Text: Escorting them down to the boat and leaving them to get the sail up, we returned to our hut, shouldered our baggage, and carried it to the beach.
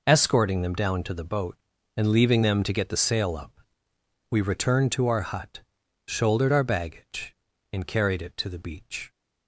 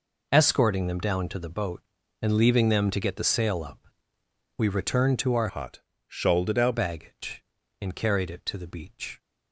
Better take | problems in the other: first | changes voice from "hut" to "our"; from 5.4 to 6.7 s; 1.3 s long

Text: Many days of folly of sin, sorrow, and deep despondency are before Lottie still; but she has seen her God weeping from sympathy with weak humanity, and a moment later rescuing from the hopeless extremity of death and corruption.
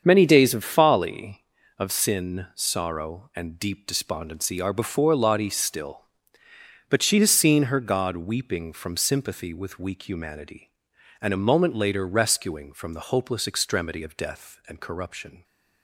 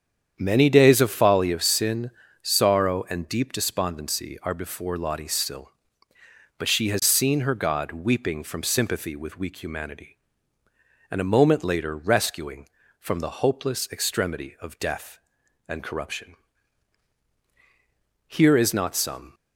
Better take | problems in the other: first | starts louder than the rest; strong; until 1.3 s; 8.5 dB; strong in the first // goes on to say "Here is not some"; noticeable; from 18.3 s on; 1.0 s long

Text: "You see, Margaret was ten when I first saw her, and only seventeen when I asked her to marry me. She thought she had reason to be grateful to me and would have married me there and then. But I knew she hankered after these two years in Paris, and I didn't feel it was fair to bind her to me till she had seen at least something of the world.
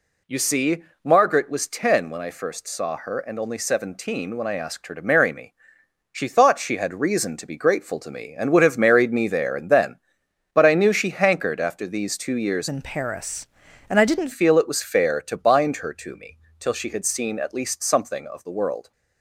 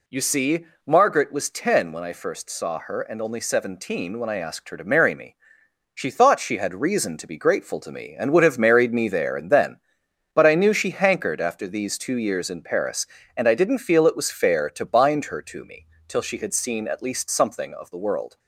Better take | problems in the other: second | changes voice from "in" to "didn't"; from 12.6 to 14.3 s; 1.7 s long // pauses between "me" and "till"; slight; at 16.3 s; 0.20 s long; slight in the second

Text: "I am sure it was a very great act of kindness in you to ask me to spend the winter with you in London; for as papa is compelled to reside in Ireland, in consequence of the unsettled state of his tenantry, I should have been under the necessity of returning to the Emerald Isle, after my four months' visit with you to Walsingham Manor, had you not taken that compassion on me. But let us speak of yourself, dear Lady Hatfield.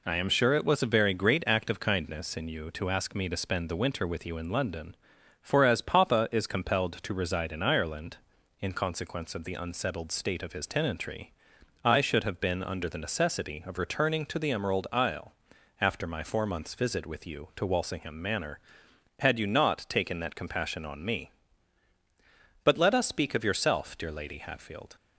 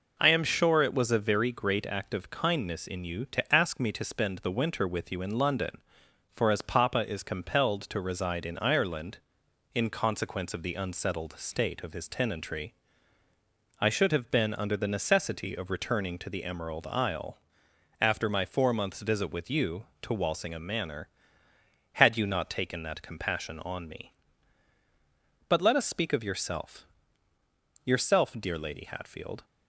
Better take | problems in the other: first | says "yourself" twice; at 27.8 s

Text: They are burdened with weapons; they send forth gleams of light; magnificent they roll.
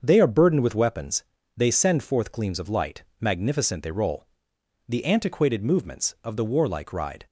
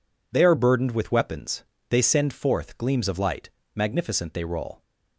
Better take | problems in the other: second | starts louder than the rest; until 1.0 s; 6.5 dB // goes on to say "The antiquated movements of the warlike ride"; strong; from 4.8 s on; 2.3 s long

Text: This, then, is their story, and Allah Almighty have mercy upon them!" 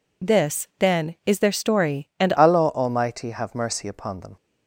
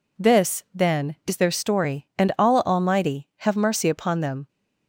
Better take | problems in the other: second | changes voice at "Allah"; from 2.3 s on; 2.0 s long

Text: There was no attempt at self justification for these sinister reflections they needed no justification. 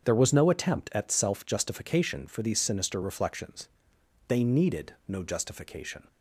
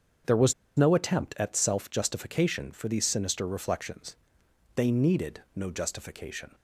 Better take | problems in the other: first | starts louder than the rest; until 1.5 s; 7 dB; strong in the first // pauses between "was" and "no"; slight; at 0.5 s; 0.25 s long // pauses between "reflections" and "they"; noticeable; at 4.1 s; 0.62 s long; noticeable in the first

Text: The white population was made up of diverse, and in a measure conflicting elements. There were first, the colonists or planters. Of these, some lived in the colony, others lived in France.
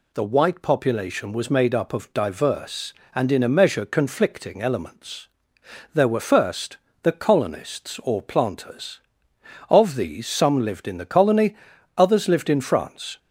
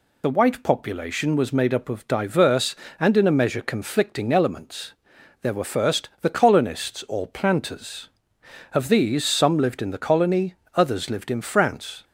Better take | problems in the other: first | loses the start of "The"; at 0.2 s; 40 ms

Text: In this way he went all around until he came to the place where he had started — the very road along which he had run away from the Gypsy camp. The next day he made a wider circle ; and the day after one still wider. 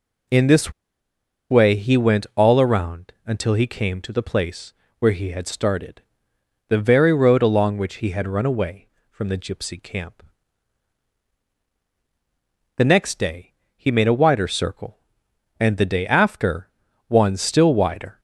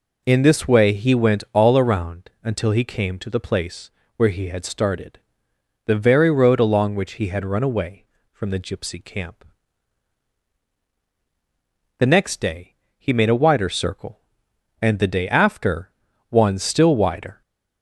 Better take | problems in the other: second | pauses between "this" and "way"; noticeable; at 0.7 s; 0.78 s long // pauses between "place" and "where"; slight; at 4.7 s; 0.26 s long; slight in the second // pauses between "day" and "he"; slight; at 13.5 s; 0.22 s long; slight in the second // pauses between "after" and "one"; at 16.6 s; 0.38 s long; also in the second

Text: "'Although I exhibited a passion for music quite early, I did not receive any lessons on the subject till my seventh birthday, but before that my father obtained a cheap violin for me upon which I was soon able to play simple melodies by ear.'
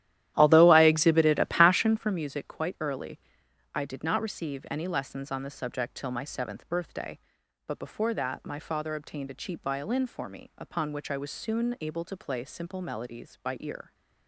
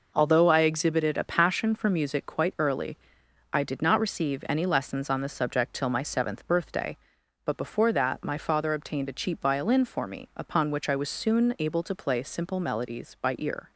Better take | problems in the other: second | starts louder than the rest; strong; until 2.2 s; 13 dB

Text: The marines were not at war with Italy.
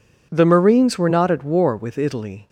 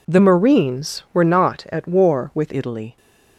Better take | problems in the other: first | changes voice from "marines" to "with"; from 0.1 to 2.5 s; 2.4 s long

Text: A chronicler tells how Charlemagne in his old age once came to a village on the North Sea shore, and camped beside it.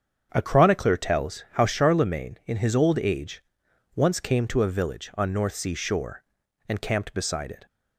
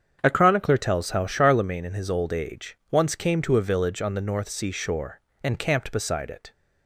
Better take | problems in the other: second | starts louder than the rest; strong; until 1.3 s; 7.5 dB; strong in the second // pauses between "age" and "once"; noticeable; at 3.4 s; 0.54 s long // skips "the"; at 5.3 s

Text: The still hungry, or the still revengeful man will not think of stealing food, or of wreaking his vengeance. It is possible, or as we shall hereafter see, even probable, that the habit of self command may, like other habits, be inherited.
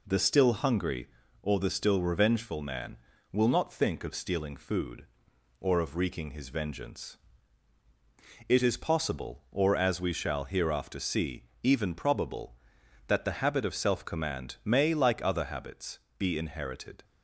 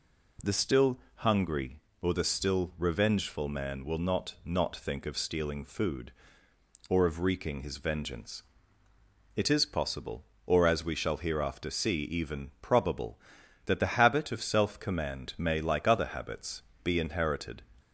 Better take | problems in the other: first | pauses between "still" and "hungry"; slight; at 0.9 s; 0.18 s long // says "not" twice; at 4.4 s

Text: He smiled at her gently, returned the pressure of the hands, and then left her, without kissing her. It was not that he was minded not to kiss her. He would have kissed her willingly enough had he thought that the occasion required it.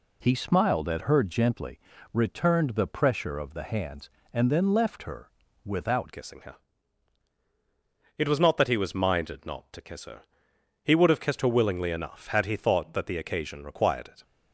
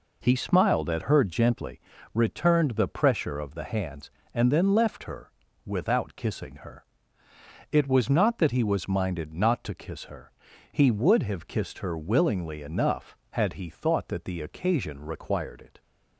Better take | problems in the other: second | changes voice at "kissing"; from 6.1 s on; 8.1 s long

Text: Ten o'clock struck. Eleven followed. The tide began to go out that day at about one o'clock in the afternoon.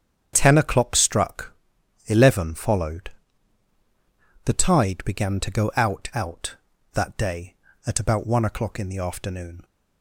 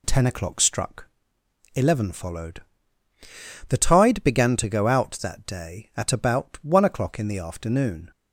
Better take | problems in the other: second | starts louder than the rest; strong; until 1.3 s; 8 dB // says "out" twice; at 6.1 s

